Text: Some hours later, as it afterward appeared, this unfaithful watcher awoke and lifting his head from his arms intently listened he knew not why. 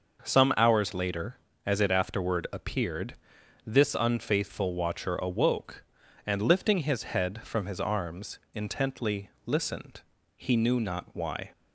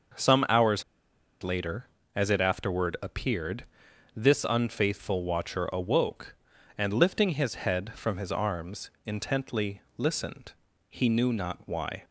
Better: first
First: starts louder than the rest; noticeable; until 1.2 s; 6 dB // pauses between "intently" and "listened"; slight; at 9.3 s; 0.16 s long // pauses between "listened" and "he"; at 10.0 s; 0.38 s long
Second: starts louder than the rest; noticeable; until 1.7 s; 6 dB // pauses between "hours" and "later"; noticeable; at 0.8 s; 0.58 s long // pauses between "intently" and "listened"; slight; at 9.8 s; 0.16 s long // pauses between "listened" and "he"; at 10.5 s; 0.40 s long

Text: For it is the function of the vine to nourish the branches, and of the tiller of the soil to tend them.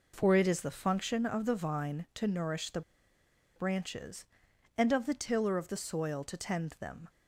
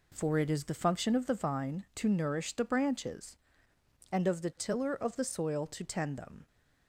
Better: second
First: pauses between "the" and "branches"; noticeable; at 2.8 s; 0.75 s long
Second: none

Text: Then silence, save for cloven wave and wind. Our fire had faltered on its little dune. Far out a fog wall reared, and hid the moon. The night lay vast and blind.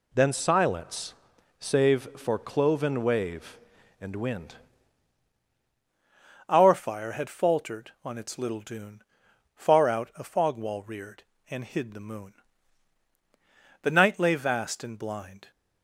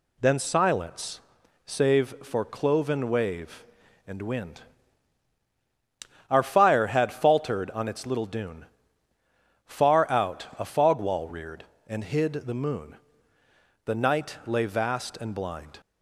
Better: second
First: changes voice at "Our"; from 6.4 s on; 9.1 s long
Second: none

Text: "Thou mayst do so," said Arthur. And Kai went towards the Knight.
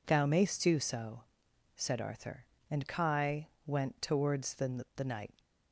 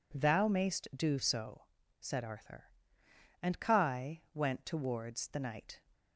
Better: second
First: pauses between "Kai" and "went"; slight; at 3.4 s; 0.16 s long // says "the" twice; at 4.9 s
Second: none

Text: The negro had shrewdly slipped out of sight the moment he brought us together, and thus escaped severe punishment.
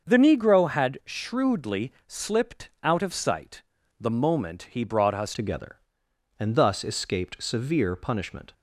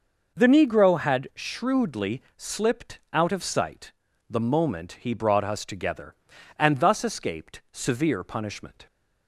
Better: second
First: starts louder than the rest; until 1.1 s; 6.5 dB // pauses between "sight" and "the"; slight; at 3.6 s; 0.36 s long // changes voice at "together"; from 5.3 s on; 3.2 s long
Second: pauses between "sight" and "the"; slight; at 3.9 s; 0.36 s long

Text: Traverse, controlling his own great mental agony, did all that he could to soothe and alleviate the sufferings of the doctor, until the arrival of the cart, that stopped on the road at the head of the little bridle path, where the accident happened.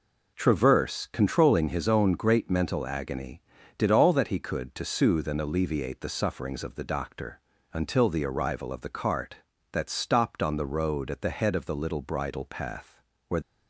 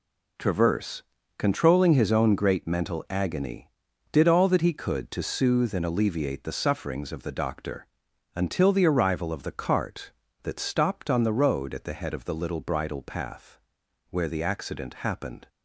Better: second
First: stops before "the accident happened"; at 13.4 s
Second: none

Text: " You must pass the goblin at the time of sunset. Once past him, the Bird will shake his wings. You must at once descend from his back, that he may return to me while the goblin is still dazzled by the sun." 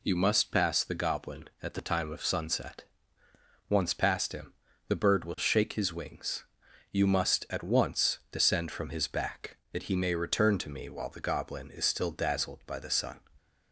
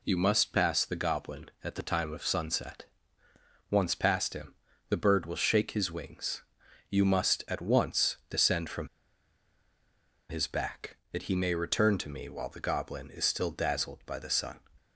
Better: first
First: none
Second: pauses between "from" and "his"; strong; at 8.8 s; 1.4 s long

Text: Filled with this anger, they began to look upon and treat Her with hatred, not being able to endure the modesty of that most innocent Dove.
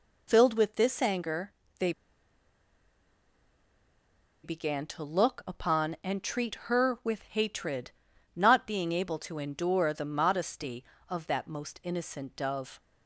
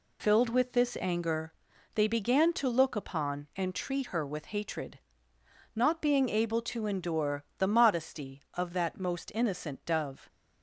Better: second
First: pauses between "they" and "began"; strong; at 1.9 s; 2.5 s long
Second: none

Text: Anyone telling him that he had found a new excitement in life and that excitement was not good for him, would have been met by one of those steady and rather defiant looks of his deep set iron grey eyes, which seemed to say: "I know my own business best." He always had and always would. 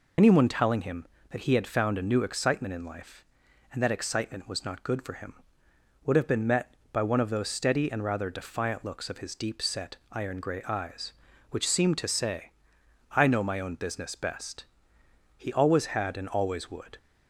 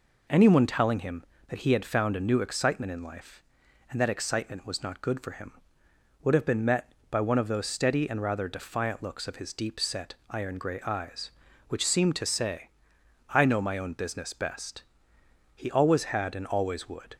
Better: second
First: loses the start of "Anyone"; at 0.1 s; 70 ms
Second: none

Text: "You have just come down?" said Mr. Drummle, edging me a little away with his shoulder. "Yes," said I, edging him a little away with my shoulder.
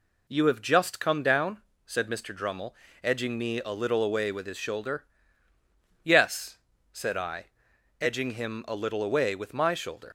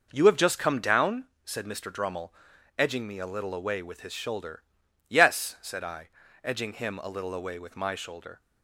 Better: second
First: leaves "shoulder" unfinished; at 10.0 s; 75 ms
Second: none

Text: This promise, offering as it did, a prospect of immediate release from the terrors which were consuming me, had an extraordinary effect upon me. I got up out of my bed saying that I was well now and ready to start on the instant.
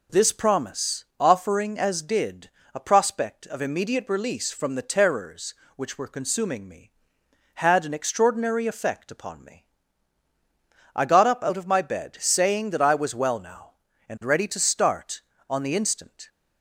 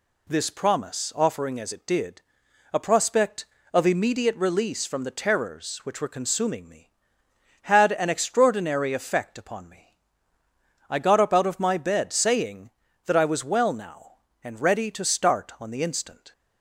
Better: second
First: skips "it"; at 2.0 s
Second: none

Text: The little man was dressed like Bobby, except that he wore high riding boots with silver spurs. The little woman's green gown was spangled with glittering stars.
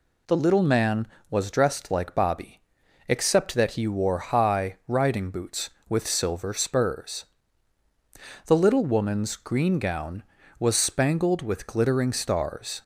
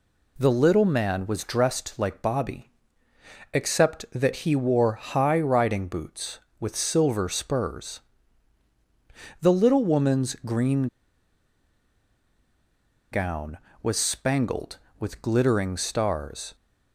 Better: first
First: none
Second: pauses between "green" and "gown"; strong; at 10.8 s; 2.2 s long

